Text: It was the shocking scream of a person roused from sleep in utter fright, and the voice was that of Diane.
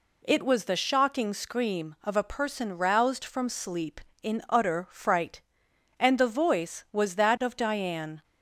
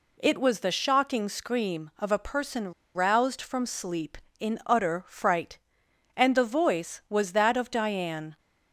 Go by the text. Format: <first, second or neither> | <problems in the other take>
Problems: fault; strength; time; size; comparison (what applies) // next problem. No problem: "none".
first | pauses between "person" and "roused"; slight; at 2.7 s; 0.22 s long